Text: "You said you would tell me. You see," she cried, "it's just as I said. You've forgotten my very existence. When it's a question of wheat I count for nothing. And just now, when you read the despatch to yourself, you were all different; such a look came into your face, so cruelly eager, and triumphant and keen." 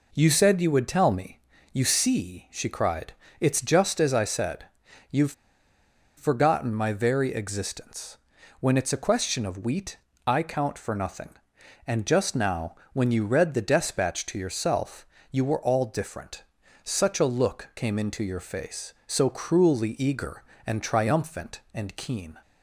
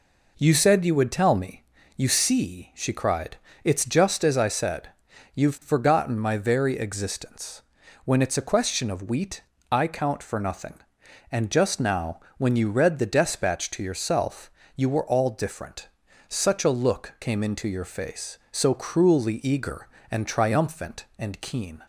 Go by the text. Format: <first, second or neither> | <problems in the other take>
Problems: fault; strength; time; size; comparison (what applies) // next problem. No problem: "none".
second | pauses between "You've" and "forgotten"; noticeable; at 5.3 s; 0.85 s long // pauses between "wheat" and "I"; slight; at 9.9 s; 0.30 s long; slight in the second